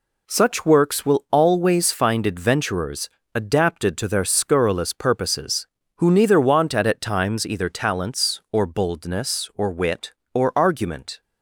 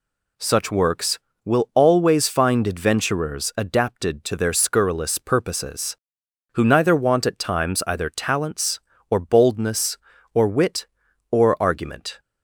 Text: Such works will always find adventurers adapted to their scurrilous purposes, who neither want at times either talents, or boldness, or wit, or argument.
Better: second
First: pauses between "adventurers" and "adapted"; slight; at 3.0 s; 0.26 s long // says "at" twice; at 6.8 s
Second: none

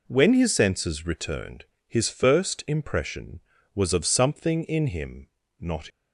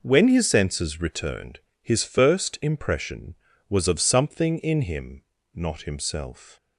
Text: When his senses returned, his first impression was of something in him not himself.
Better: second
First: pauses between "him" and "not"; slight; at 5.2 s; 0.32 s long // stops before "himself"; at 5.8 s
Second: pauses between "him" and "not"; slight; at 5.2 s; 0.32 s long

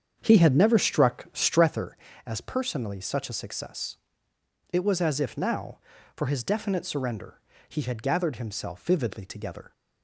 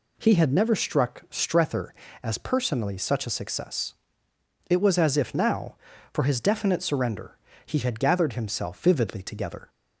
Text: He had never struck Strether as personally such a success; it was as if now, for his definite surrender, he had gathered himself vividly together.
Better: second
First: starts louder than the rest; strong; until 1.9 s; 7.5 dB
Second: none

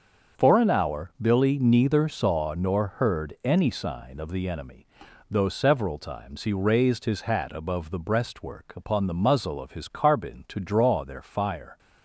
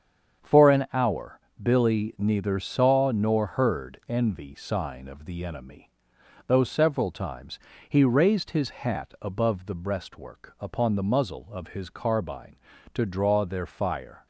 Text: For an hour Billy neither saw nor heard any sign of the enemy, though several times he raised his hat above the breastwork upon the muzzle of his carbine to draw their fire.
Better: first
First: starts louder than the rest; until 1.4 s; 6.5 dB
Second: starts louder than the rest; strong; until 1.6 s; 7.5 dB // pauses between "hour" and "Billy"; slight; at 1.3 s; 0.20 s long // says "envy" for "any"; at 4.0 s // pauses between "times" and "he"; slight; at 7.5 s; 0.32 s long

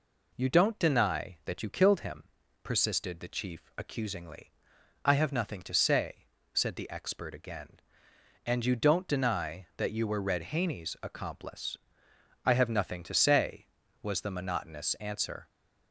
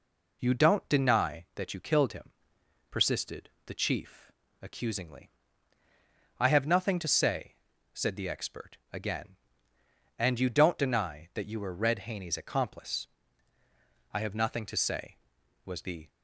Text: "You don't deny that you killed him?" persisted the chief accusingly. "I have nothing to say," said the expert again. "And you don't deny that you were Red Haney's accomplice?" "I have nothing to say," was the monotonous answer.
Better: first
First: none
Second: pauses between "persisted" and "the"; slight; at 3.5 s; 0.16 s long // pauses between "chief" and "accusingly"; slight; at 4.3 s; 0.30 s long // stops before "monotonous answer"; at 16.0 s

